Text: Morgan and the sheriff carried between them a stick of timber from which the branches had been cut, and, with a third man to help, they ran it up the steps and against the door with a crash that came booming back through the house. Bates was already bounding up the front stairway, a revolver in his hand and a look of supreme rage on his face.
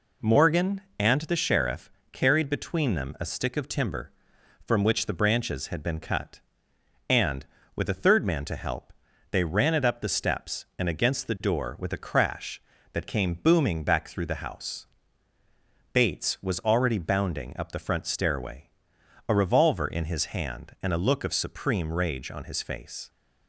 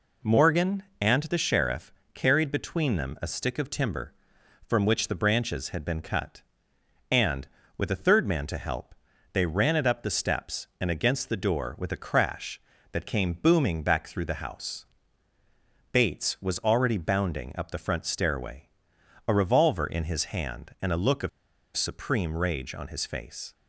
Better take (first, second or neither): first